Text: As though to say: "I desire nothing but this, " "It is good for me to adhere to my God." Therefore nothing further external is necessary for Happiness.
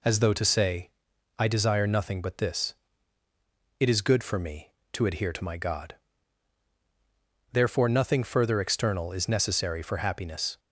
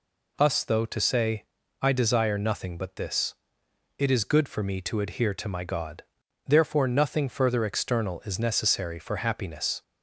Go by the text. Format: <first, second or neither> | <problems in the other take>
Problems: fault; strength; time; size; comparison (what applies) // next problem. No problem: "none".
first | says "Us" for "As"; at 0.3 s